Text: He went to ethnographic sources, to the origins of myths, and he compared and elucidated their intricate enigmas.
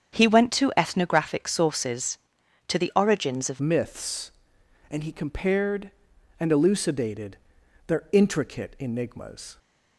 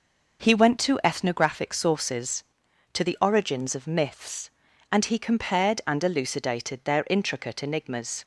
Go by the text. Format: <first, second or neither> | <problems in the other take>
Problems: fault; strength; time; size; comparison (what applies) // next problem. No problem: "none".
second | starts louder than the rest; strong; until 1.2 s; 8 dB // changes voice at "myths"; from 3.5 s on; 6.0 s long // pauses between "elucidated" and "their"; noticeable; at 7.3 s; 0.52 s long